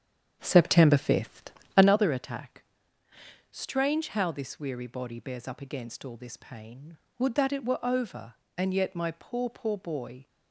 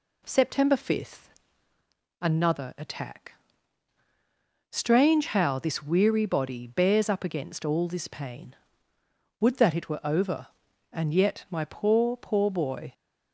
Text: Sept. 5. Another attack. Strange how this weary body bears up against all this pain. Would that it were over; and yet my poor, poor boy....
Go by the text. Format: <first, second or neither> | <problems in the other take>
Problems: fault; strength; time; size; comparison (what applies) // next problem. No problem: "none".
second | starts louder than the rest; strong; until 1.9 s; 8 dB